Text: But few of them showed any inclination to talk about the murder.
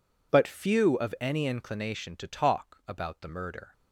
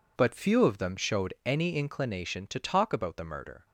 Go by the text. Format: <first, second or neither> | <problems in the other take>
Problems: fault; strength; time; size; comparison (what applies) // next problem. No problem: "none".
second | skips "them showed"; at 1.1 s